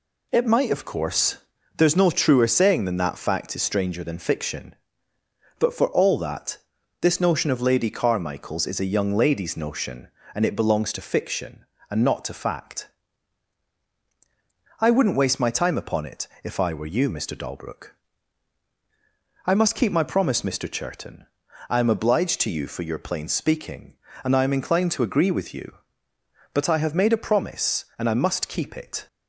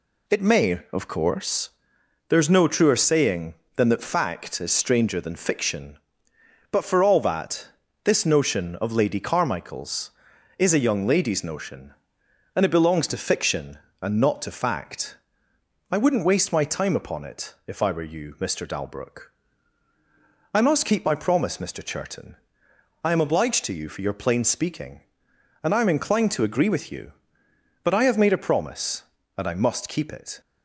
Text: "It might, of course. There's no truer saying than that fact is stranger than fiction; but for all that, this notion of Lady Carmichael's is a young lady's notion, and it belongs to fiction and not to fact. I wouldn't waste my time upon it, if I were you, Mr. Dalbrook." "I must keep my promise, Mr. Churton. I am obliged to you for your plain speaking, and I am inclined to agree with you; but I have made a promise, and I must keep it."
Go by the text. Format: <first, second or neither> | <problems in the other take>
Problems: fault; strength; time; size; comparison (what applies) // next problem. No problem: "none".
first | says "may" for "might"; at 0.4 s